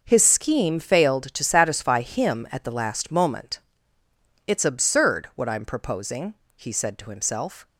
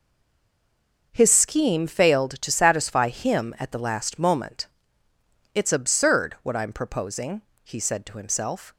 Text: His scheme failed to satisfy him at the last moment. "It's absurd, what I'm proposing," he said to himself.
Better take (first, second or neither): first